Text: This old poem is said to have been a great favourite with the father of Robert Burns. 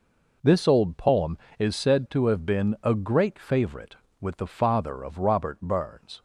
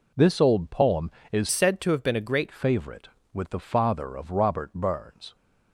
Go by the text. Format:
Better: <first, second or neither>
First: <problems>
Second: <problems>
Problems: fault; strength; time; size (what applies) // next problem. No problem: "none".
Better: first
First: none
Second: changes voice from "said" to "great"; from 1.5 to 2.4 s; 0.9 s long